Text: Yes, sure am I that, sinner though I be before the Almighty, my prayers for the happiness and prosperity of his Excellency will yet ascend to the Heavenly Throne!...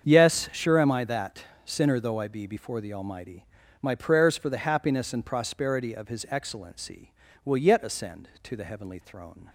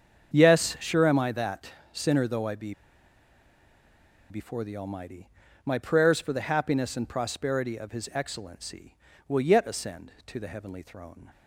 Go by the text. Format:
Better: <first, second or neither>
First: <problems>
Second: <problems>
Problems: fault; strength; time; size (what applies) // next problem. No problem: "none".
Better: first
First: starts louder than the rest; strong; until 1.1 s; 7 dB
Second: starts louder than the rest; strong; until 1.3 s; 7 dB // pauses between "be" and "before"; strong; at 2.7 s; 1.5 s long